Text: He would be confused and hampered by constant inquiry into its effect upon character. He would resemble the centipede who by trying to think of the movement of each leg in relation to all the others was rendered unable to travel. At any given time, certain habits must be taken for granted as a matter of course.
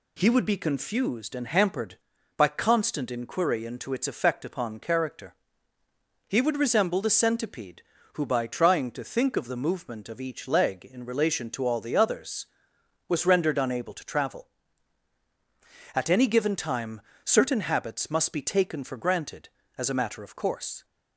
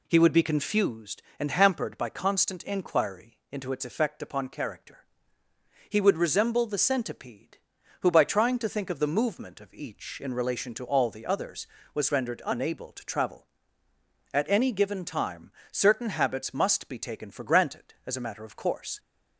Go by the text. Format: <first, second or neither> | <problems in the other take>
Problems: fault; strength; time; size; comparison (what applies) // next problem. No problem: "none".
first | skips "leg"; at 10.2 s